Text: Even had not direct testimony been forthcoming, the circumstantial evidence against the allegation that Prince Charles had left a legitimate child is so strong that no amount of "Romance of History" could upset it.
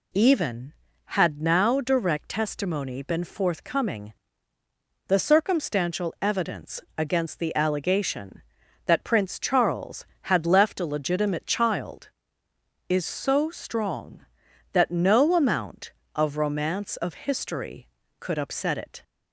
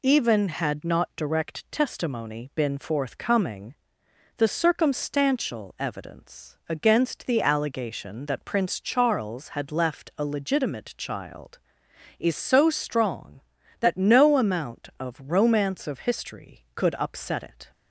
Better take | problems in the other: second | says "now" for "not"; at 1.4 s // pauses between "evidence" and "against"; slight; at 6.8 s; 0.16 s long

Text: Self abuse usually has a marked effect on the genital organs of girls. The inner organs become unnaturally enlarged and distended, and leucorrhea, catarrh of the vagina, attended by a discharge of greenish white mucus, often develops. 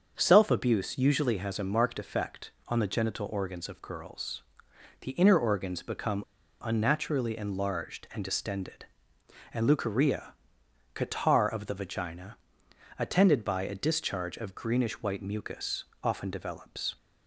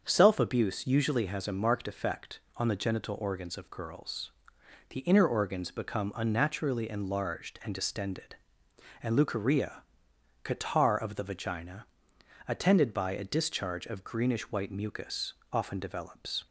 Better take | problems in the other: second | starts louder than the rest; until 1.1 s; 7 dB; also in the second // pauses between "become" and "unnaturally"; at 6.2 s; 0.38 s long

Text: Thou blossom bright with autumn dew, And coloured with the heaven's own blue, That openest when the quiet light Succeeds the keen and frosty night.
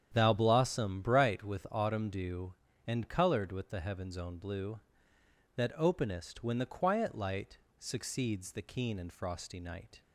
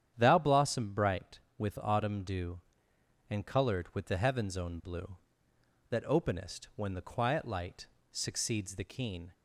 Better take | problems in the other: first | starts louder than the rest; strong; until 1.1 s; 9.5 dB; strong in the first // pauses between "light" and "Succeeds"; slight; at 7.8 s; 0.24 s long; slight in the first // stops before "and frosty night"; at 9.3 s

